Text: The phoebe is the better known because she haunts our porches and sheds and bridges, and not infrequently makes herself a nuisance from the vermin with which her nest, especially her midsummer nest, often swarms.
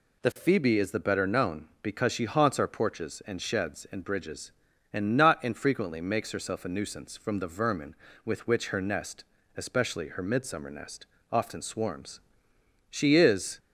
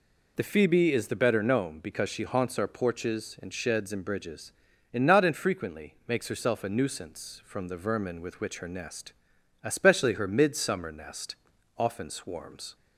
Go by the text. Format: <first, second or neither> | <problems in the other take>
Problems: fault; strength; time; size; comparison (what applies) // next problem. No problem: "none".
second | goes on to say "She is"; noticeable; from 12.8 s on; 0.70 s long